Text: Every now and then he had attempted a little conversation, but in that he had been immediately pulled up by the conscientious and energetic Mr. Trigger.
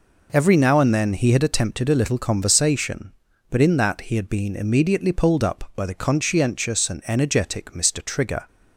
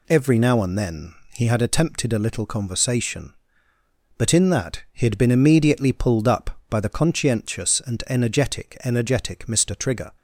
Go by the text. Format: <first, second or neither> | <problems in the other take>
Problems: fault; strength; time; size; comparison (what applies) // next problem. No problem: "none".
first | pauses between "then" and "he"; slight; at 1.1 s; 0.18 s long // says "energetic" twice; at 8.8 s